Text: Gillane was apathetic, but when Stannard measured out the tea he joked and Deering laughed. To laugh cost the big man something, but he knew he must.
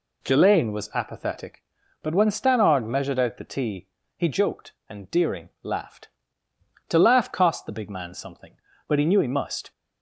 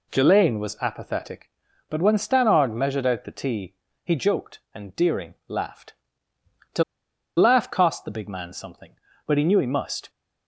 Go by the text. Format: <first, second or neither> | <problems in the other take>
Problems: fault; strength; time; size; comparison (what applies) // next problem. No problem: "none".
first | pauses between "tea" and "he"; slight; at 3.7 s; 0.30 s long; slight in the first // pauses between "To" and "laugh"; noticeable; at 6.8 s; 0.54 s long